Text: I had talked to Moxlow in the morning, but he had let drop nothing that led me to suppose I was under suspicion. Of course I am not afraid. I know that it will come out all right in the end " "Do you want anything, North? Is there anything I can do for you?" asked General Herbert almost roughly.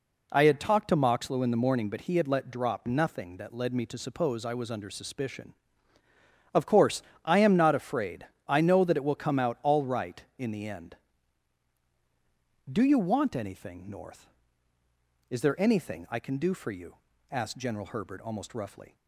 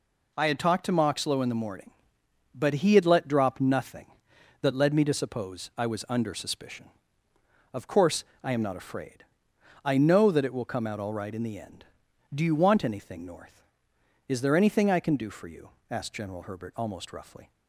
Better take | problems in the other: neither | pauses between "course" and "I"; slight; the same in both

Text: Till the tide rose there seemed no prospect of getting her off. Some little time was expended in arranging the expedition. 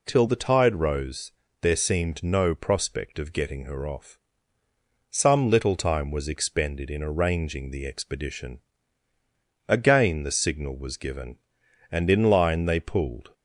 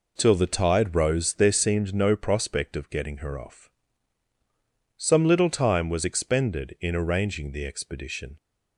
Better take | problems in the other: second | pauses between "rose" and "there"; slight; at 1.3 s; 0.30 s long // goes on to say "Again the signal was given and in line they pulled"; strong; from 9.6 s on; 3.6 s long

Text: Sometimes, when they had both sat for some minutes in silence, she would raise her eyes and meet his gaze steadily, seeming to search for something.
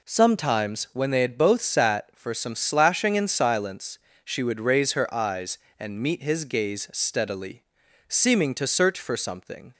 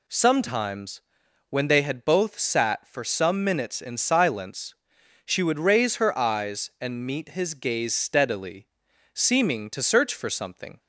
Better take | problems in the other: second | says "slashing" for "minutes"; at 2.5 s

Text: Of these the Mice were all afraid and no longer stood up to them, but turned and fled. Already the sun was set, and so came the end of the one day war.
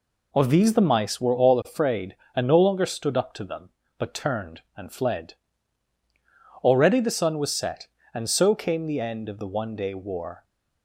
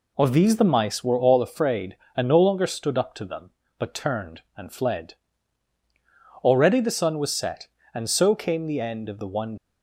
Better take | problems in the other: first | stops before "day war"; at 9.5 s

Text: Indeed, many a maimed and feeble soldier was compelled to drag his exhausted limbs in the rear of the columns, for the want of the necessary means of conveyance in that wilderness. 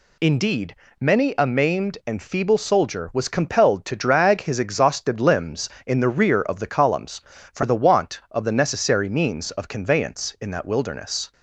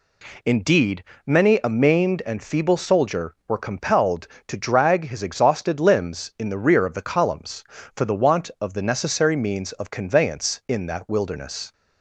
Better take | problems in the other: first | says "were" for "was"; at 3.4 s

